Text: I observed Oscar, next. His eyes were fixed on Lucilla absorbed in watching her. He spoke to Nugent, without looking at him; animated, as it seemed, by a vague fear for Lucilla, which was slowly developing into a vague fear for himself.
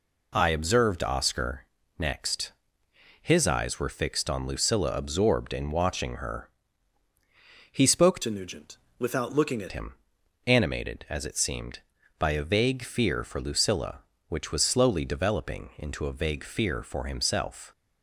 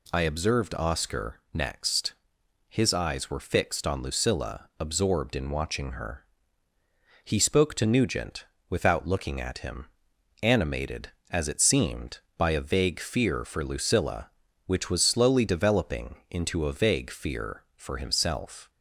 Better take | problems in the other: second | changes voice from "to" to "at"; from 8.2 to 9.7 s; 1.5 s long

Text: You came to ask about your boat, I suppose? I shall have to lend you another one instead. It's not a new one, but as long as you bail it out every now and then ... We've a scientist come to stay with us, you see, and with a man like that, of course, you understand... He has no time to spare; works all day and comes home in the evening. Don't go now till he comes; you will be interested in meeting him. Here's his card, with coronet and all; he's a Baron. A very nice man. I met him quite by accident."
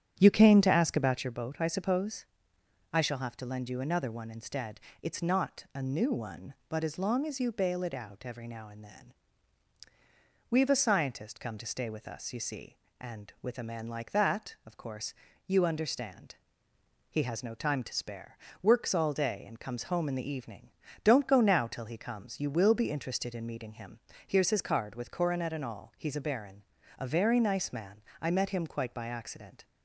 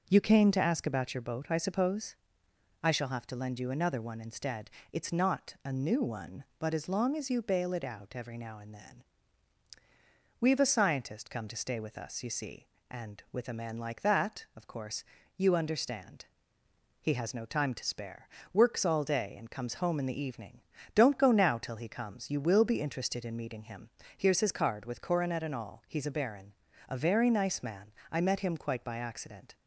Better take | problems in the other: second | starts louder than the rest; strong; until 1.4 s; 9 dB

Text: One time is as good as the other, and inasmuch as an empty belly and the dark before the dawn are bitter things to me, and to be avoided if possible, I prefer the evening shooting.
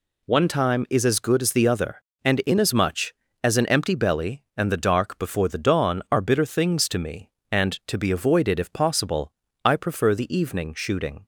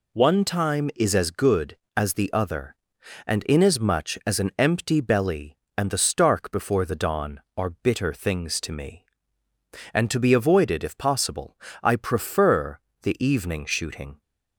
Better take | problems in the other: first | says "stark" for "dark"; at 5.9 s // pauses between "prefer" and "the"; slight; at 12.8 s; 0.22 s long

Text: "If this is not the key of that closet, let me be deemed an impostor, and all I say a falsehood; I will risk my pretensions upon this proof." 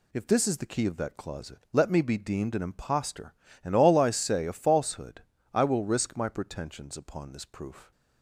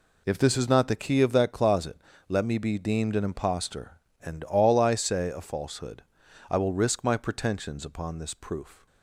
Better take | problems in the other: second | skips "not"; at 0.5 s

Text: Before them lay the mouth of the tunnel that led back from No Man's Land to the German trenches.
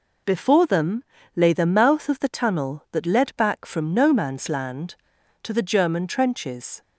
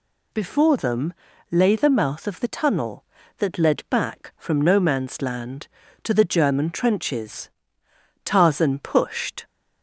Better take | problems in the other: first | pauses between "them" and "lay"; at 1.1 s; 0.38 s long; slight in the first // goes on to say "Tarzan pushed"; noticeable; from 8.2 s on; 1.2 s long

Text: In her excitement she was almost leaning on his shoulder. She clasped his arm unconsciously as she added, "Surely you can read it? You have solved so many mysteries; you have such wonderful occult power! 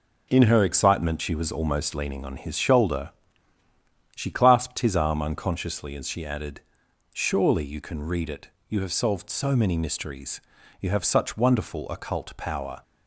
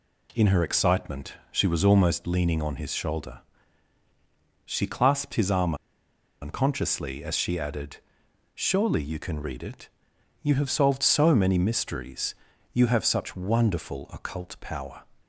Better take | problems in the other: first | pauses between "excitement" and "she"; slight; at 1.3 s; 0.16 s long // pauses between "arm" and "unconsciously"; noticeable; at 5.7 s; 0.66 s long

